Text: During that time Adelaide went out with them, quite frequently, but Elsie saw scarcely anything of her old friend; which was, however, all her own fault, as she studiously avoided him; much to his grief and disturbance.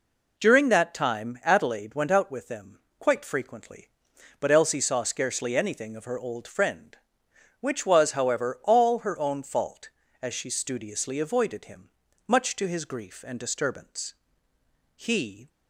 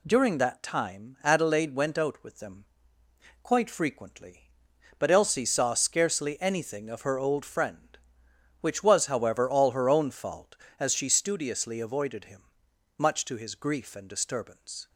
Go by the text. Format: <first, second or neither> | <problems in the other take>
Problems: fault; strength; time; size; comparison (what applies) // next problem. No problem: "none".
second | goes on to say "He"; from 14.9 s on; 0.54 s long